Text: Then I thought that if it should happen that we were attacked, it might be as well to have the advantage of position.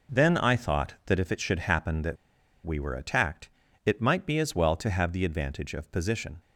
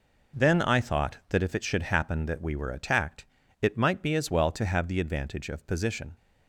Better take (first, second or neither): second